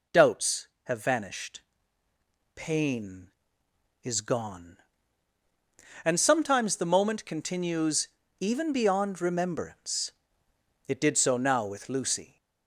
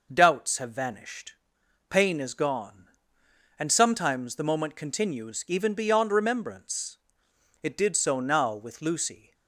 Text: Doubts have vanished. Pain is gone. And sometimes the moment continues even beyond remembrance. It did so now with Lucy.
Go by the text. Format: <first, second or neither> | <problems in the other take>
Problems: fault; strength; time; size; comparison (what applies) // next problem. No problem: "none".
second | gets louder; slight; throughout; 3 dB // pauses between "continues" and "even"; slight; at 8.0 s; 0.32 s long